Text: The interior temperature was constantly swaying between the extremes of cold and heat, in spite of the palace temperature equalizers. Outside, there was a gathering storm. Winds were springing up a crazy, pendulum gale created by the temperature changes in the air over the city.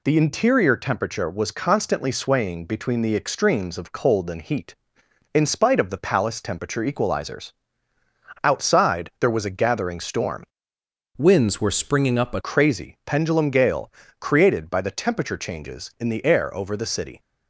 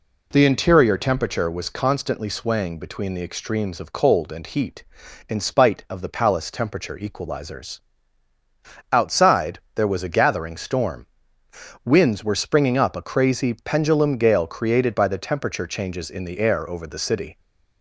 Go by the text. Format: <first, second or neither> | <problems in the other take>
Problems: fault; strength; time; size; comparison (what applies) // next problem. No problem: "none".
second | changes voice from "Winds" to "a"; from 11.1 to 12.3 s; 1.2 s long // pauses between "gale" and "created"; slight; at 13.9 s; 0.28 s long